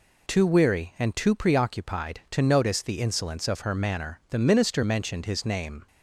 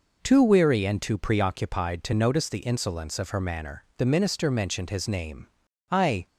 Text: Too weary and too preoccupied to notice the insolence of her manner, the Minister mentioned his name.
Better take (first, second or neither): first